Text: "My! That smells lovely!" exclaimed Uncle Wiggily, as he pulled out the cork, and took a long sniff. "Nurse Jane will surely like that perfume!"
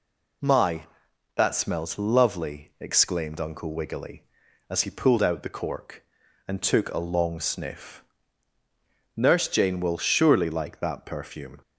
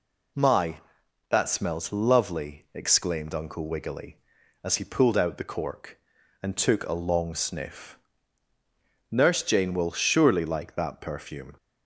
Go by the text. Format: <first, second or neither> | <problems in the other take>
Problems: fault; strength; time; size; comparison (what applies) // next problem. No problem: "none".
neither | none